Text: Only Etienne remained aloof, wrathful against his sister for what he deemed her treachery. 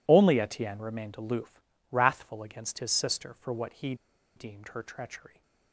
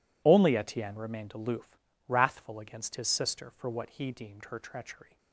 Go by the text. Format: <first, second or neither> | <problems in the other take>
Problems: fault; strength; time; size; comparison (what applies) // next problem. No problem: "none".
second | pauses between "he" and "deemed"; at 3.9 s; 0.41 s long